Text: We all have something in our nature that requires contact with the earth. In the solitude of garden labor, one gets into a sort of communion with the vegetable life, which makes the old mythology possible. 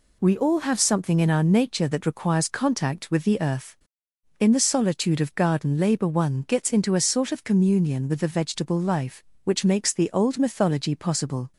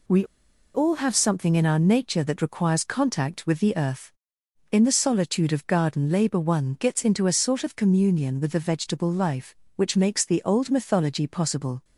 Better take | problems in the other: first | pauses between "We" and "all"; noticeable; at 0.2 s; 0.50 s long

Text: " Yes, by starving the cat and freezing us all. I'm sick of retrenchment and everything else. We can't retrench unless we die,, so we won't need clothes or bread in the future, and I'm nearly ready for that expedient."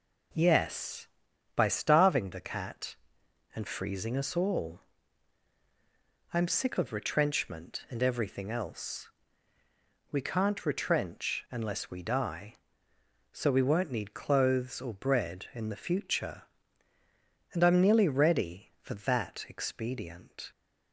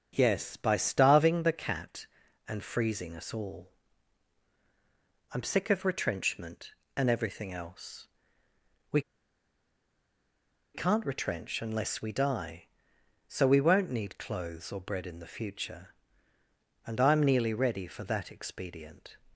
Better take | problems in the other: first | starts louder than the rest; until 1.1 s; 6.5 dB // pauses between "We" and "can't"; strong; at 9.0 s; 1.7 s long

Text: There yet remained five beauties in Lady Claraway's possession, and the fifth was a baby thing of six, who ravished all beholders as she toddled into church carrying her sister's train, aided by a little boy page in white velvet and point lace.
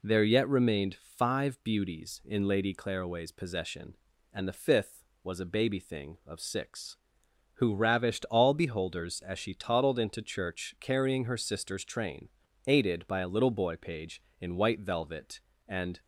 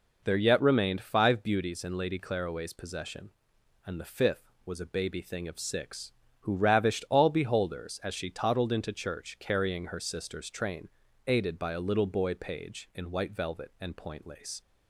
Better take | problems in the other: second | stops before "point lace"; at 16.0 s

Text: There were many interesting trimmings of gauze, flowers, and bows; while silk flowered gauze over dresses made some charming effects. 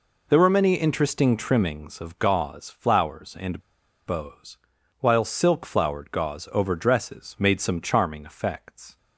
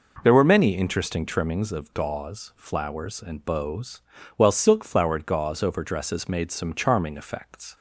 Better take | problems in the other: second | pauses between "and" and "bows"; noticeable; at 3.5 s; 0.47 s long

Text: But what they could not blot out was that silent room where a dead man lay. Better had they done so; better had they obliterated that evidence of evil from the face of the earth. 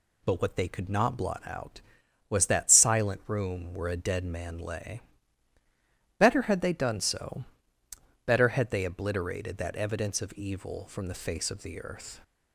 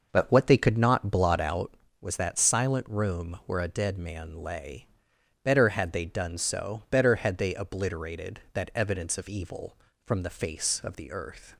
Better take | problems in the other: first | starts louder than the rest; noticeable; until 1.8 s; 6 dB

